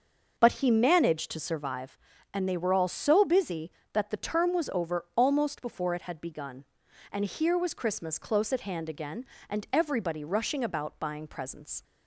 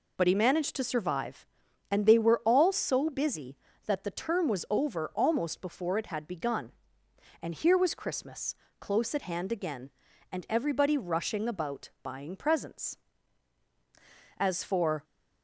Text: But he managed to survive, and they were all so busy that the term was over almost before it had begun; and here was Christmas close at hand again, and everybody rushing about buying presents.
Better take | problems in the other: first | pauses between "Christmas" and "close"; slight; at 8.5 s; 0.24 s long // pauses between "about" and "buying"; slight; at 11.8 s; 0.16 s long // goes on to say "As for"; noticeable; from 14.3 s on; 0.66 s long

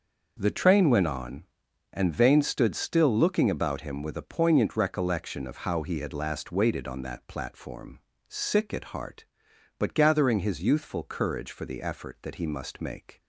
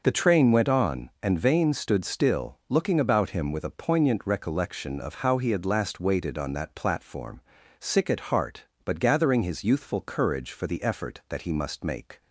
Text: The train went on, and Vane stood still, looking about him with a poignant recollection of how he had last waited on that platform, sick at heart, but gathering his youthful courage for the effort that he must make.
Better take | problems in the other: neither | none

